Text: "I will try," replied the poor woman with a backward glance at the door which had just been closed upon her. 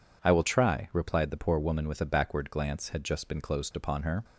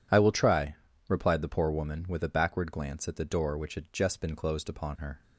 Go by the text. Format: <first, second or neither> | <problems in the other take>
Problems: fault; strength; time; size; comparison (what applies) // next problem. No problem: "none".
second | skips "at the door which"; at 2.8 s